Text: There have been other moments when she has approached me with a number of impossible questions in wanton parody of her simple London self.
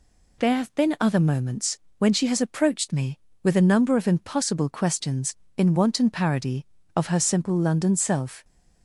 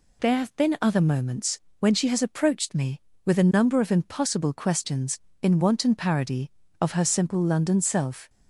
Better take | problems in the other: neither | pauses between "moments" and "when"; slight; the same in both

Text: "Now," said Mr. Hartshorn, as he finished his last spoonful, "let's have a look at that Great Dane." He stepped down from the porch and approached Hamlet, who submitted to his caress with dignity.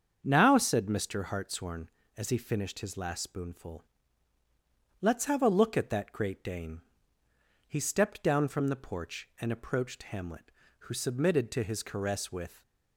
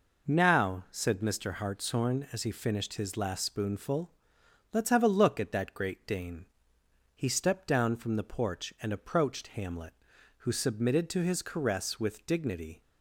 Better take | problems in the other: second | starts louder than the rest; strong; until 1.2 s; 7 dB // stops before "dignity"; at 12.6 s

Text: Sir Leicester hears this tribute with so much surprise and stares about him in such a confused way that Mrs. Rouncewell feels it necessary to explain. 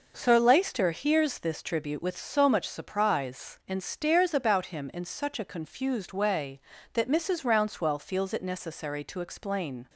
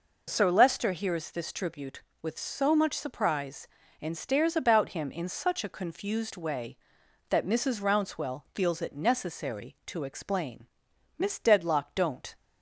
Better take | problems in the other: first | goes on to say "Miss Dedlock don't"; noticeable; from 11.1 s on; 1.1 s long

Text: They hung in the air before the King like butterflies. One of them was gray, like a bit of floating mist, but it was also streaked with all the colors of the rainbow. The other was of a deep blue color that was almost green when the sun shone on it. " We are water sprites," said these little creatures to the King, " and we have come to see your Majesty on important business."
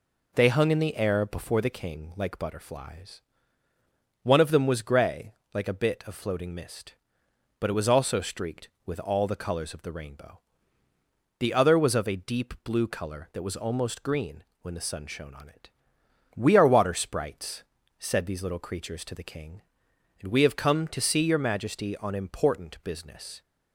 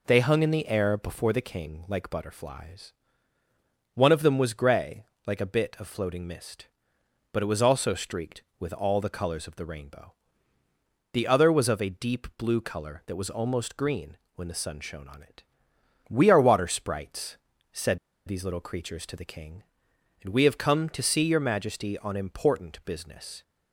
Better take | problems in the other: first | pauses between "green" and "when"; slight; at 14.1 s; 0.18 s long; slight in the first // pauses between "said" and "these"; slight; at 17.9 s; 0.28 s long

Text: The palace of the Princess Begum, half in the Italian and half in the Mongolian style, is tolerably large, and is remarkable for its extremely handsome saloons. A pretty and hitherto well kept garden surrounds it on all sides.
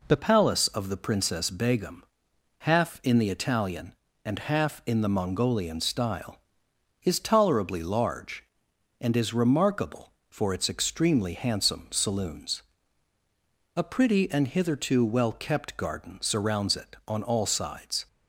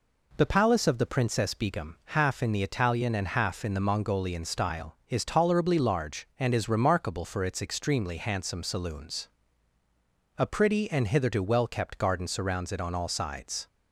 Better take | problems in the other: second | changes voice at "palace"; from 0.1 s on; 17.9 s long

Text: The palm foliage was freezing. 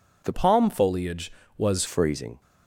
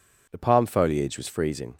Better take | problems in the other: second | changes voice from "palm" to "was"; from 0.3 to 1.8 s; 1.5 s long

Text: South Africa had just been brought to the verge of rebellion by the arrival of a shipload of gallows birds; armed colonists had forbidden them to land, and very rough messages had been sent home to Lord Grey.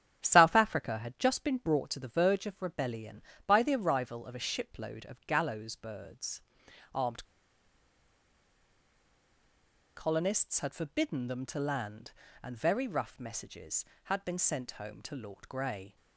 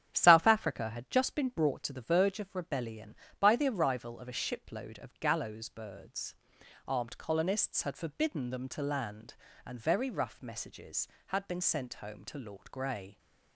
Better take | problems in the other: second | starts louder than the rest; strong; until 1.2 s; 9 dB; strong in the second // pauses between "armed" and "colonists"; strong; at 7.2 s; 2.7 s long

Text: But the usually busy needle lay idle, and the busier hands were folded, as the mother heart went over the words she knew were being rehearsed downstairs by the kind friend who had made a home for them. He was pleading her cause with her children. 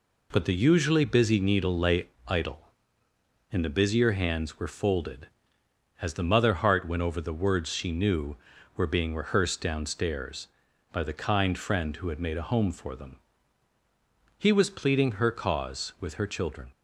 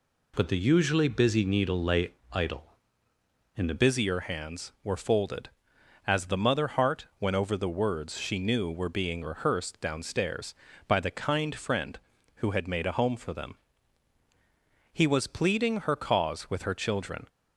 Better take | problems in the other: first | pauses between "lay" and "idle"; slight; at 2.1 s; 0.18 s long; slight in the first // changes voice at "busier"; from 3.7 s on; 13.5 s long

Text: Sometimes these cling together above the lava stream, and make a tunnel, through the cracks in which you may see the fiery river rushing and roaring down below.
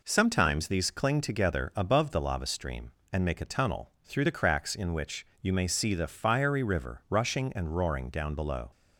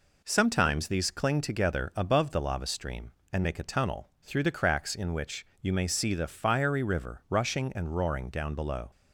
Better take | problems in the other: neither | none

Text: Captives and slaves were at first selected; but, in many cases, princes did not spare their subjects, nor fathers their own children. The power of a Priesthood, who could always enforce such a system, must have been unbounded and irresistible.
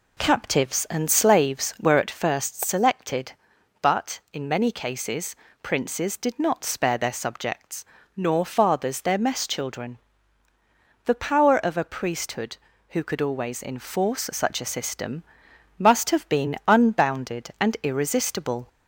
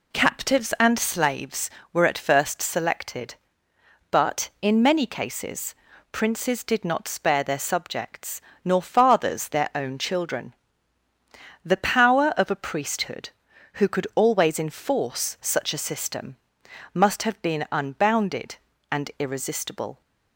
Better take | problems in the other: second | says "mess" for "own"; at 9.1 s

